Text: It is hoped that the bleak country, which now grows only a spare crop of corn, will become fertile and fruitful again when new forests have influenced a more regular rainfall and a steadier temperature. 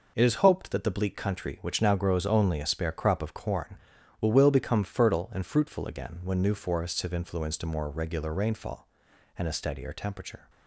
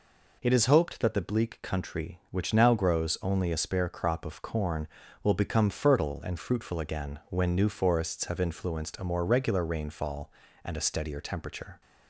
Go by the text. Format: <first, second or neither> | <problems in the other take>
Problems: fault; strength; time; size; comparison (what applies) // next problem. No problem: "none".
second | says "will" twice; at 4.3 s